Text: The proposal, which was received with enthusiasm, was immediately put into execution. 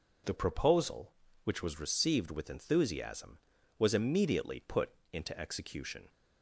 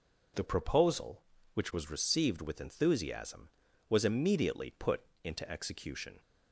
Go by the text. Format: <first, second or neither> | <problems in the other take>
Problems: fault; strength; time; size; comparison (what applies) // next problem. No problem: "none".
neither | pauses between "put" and "into"; slight; the same in both